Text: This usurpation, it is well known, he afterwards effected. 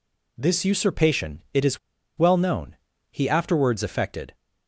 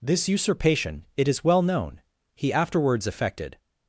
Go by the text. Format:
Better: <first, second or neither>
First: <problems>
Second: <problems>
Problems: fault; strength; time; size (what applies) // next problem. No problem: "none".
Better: second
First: pauses between "is" and "well"; at 1.7 s; 0.41 s long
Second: none